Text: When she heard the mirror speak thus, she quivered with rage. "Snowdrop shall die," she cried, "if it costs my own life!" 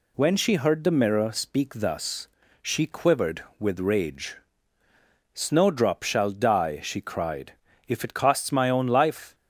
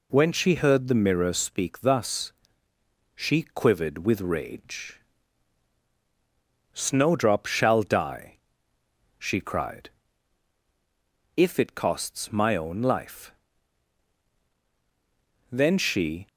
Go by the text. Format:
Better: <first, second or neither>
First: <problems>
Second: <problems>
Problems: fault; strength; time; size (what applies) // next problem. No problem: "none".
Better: first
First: none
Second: goes on to say "Then she"; noticeable; from 15.4 s on; 0.78 s long